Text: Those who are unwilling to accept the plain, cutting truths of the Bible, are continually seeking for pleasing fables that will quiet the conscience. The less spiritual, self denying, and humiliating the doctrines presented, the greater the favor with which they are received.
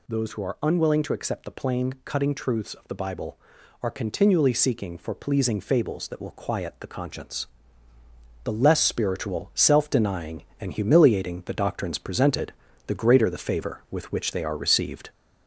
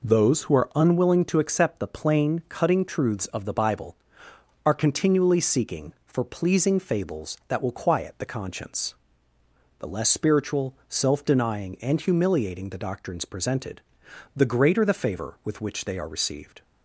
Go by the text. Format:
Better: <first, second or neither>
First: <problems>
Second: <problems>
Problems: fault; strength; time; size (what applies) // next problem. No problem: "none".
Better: second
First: gets louder; slight; throughout; 3 dB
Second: none